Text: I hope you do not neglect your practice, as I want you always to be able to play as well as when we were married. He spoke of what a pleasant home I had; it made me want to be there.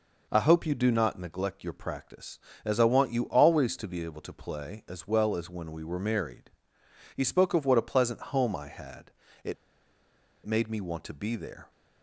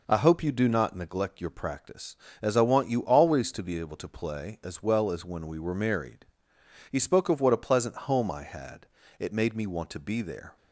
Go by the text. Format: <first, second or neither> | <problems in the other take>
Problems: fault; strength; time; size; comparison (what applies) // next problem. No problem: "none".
second | pauses between "it" and "made"; noticeable; at 9.5 s; 0.91 s long